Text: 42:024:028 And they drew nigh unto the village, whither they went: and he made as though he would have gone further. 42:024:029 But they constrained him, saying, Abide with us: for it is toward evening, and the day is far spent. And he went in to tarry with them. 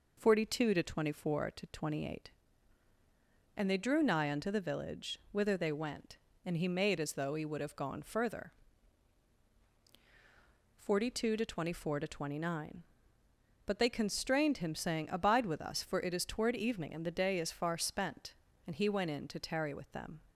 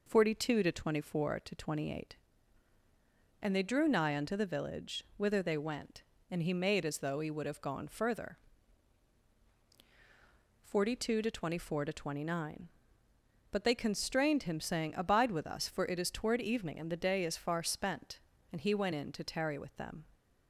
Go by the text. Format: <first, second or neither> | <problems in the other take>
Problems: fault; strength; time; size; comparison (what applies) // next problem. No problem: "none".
neither | none